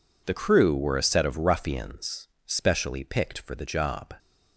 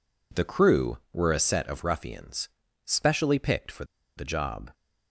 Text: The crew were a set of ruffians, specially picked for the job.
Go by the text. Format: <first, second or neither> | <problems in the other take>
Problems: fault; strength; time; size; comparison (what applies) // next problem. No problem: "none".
first | pauses between "for" and "the"; slight; at 3.8 s; 0.32 s long